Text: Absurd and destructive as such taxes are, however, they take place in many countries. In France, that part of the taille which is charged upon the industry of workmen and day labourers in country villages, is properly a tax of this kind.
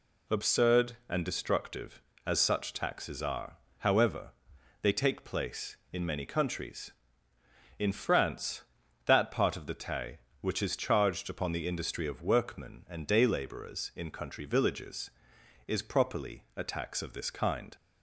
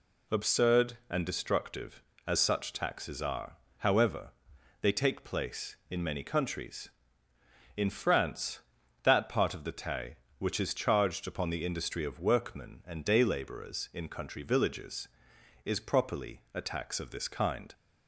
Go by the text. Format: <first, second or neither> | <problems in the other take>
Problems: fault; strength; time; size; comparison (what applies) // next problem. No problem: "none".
neither | none